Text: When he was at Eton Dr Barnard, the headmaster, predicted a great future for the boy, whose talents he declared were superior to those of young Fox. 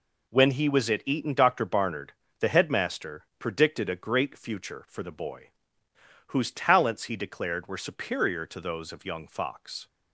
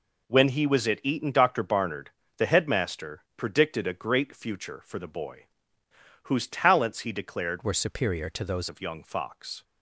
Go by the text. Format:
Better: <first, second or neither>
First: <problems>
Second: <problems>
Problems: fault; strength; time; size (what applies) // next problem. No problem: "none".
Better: first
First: none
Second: changes voice from "were" to "those"; from 7.6 to 8.6 s; 1.0 s long